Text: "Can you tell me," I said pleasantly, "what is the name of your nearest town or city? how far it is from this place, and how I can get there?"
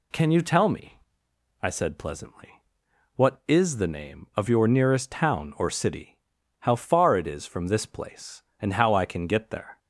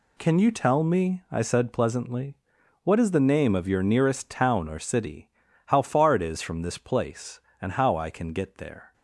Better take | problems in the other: neither | none

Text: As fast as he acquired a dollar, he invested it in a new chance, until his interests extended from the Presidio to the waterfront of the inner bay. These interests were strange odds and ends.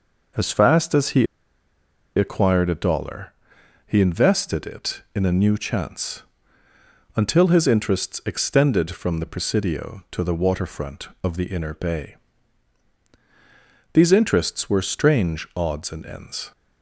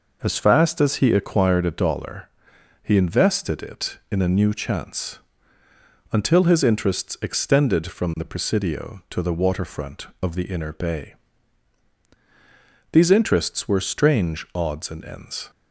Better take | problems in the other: second | pauses between "he" and "acquired"; noticeable; at 1.2 s; 0.91 s long

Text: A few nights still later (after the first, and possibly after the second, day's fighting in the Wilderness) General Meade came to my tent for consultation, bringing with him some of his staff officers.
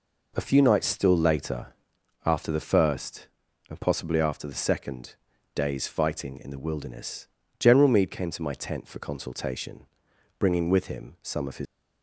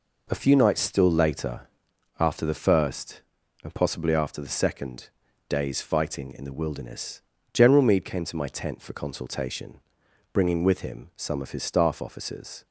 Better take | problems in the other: second | stops before "staff officers"; at 11.6 s

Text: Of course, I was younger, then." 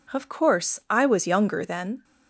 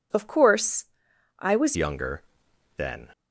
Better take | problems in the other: first | changes voice at "younger"; from 1.7 s on; 1.4 s long

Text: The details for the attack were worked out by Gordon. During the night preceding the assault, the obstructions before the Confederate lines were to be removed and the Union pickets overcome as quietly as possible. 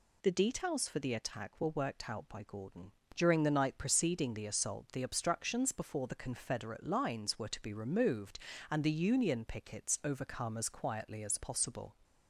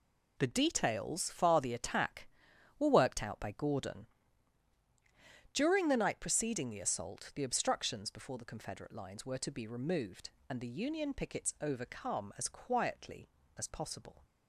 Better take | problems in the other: first | says "far" for "for"; at 1.3 s

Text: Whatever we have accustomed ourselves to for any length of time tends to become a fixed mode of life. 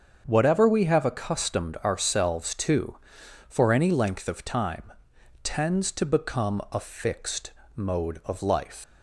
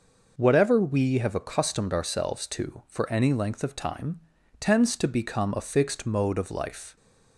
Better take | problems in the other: second | starts louder than the rest; strong; until 1.2 s; 7 dB // pauses between "time" and "tends"; noticeable; at 4.9 s; 0.52 s long; also in the second // pauses between "fixed" and "mode"; slight; at 7.5 s; 0.26 s long // leaves "life" unfinished; at 8.8 s; 65 ms

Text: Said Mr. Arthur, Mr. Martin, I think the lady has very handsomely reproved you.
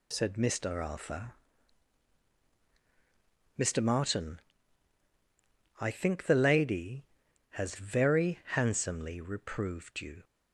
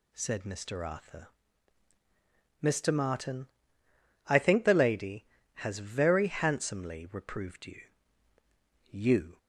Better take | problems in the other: first | says "you" twice; at 8.8 s

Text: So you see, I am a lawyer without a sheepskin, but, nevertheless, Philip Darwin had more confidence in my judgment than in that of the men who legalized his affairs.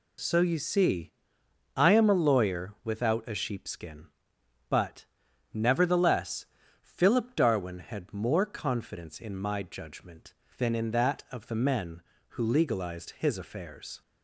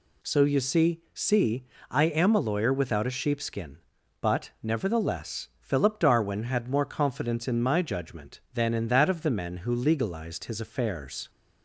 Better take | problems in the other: first | says "see" twice; at 1.1 s

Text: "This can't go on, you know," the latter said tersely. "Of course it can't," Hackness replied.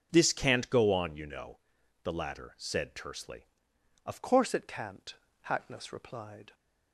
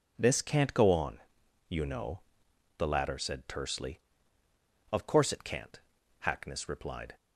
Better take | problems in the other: second | starts louder than the rest; until 1.1 s; 6 dB // changes voice at "course"; from 4.2 s on; 2.3 s long

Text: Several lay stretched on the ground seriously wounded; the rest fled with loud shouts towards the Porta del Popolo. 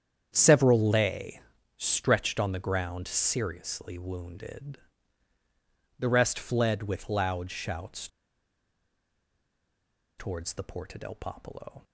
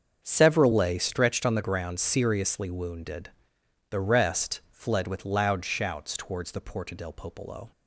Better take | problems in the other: second | starts louder than the rest; strong; until 1.3 s; 8.5 dB; also in the second // pauses between "lay" and "stretched"; slight; at 1.4 s; 0.36 s long // pauses between "shouts" and "towards"; strong; at 8.0 s; 2.1 s long

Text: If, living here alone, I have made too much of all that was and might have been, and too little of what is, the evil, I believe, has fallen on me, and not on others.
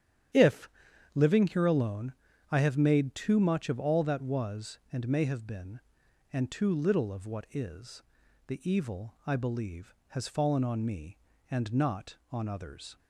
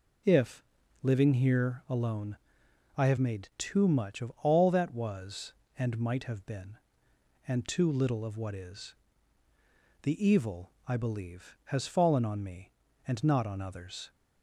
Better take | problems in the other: second | starts louder than the rest; strong; until 1.8 s; 9.5 dB // says "may" for "might"; at 5.0 s

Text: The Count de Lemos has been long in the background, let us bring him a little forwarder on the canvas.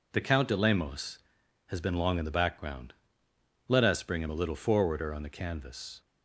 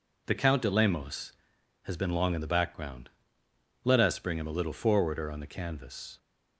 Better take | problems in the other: neither | none

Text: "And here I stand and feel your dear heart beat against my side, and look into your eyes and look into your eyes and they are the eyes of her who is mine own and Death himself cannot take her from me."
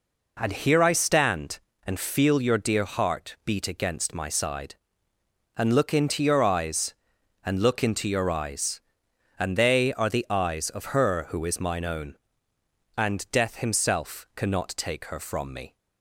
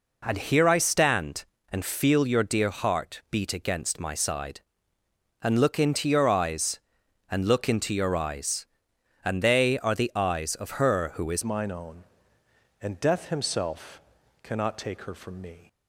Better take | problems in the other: first | changes voice at "mine"; from 11.4 s on; 4.2 s long // pauses between "himself" and "cannot"; at 14.0 s; 0.40 s long

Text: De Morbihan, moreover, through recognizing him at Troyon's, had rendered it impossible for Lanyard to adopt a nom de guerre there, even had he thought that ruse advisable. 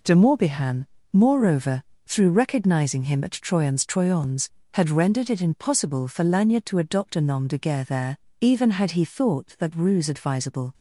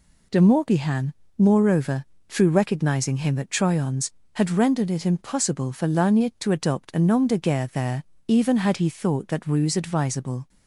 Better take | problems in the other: second | says "Troyon's" twice; at 3.8 s

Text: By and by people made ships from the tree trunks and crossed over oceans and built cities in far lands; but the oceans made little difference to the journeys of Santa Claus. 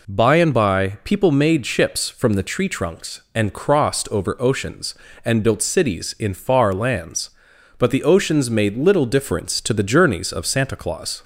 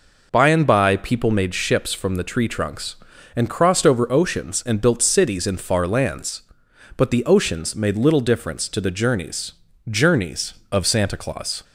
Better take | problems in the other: first | says "journeys" twice; at 9.8 s

